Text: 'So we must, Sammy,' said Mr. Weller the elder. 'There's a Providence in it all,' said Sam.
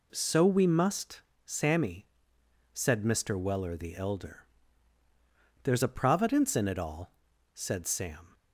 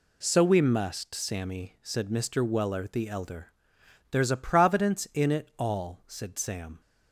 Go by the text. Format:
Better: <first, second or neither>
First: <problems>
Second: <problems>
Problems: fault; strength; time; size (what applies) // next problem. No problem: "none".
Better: neither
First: none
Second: none